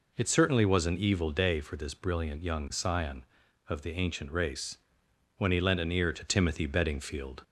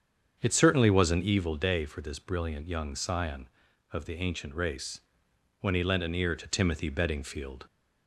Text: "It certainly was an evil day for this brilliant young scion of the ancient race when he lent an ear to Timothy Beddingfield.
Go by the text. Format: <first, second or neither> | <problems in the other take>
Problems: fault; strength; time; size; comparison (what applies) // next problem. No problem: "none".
first | starts louder than the rest; strong; until 1.5 s; 7.5 dB // pauses between "race" and "when"; noticeable; at 5.0 s; 0.60 s long; noticeable in the first